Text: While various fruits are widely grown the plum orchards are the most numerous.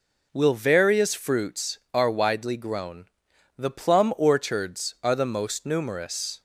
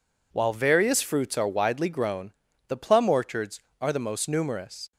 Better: second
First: says "Will" for "While"; at 0.3 s // pauses between "grown" and "the"; noticeable; at 3.0 s; 0.52 s long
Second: pauses between "grown" and "the"; at 2.3 s; 0.38 s long

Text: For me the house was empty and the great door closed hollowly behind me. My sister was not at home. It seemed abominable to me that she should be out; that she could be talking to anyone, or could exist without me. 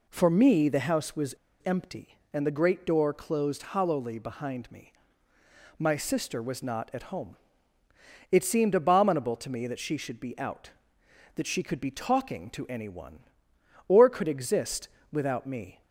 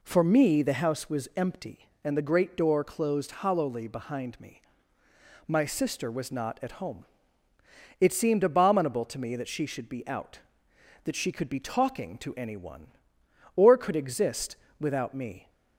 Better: second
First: pauses between "was" and "empty"; slight; at 1.3 s; 0.30 s long // pauses between "exist" and "without"; slight; at 14.8 s; 0.24 s long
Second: pauses between "exist" and "without"; slight; at 14.5 s; 0.24 s long

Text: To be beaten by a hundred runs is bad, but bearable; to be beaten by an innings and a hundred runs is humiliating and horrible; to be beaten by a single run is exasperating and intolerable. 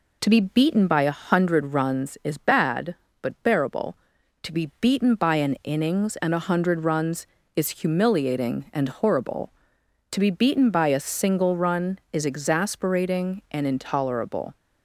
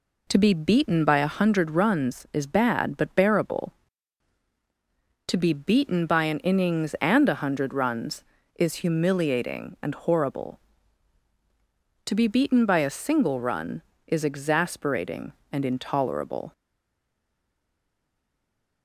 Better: first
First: none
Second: stays silent after the last word; from 16.5 s on; 2.3 s long

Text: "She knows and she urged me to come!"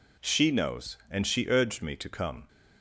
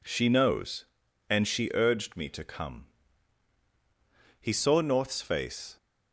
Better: first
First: none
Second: goes on to say "He saw North's face"; from 4.4 s on; 1.3 s long

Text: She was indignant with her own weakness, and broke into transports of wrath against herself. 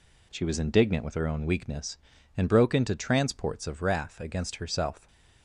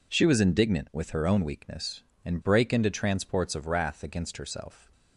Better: first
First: none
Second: says "brake" for "broke"; at 2.4 s

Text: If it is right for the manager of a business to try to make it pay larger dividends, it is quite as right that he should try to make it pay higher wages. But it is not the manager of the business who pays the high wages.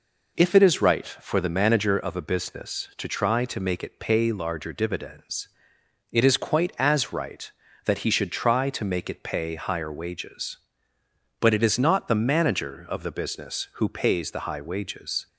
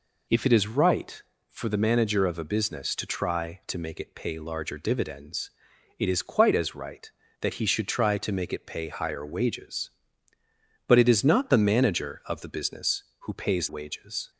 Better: first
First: none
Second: skips "the high"; at 13.6 s

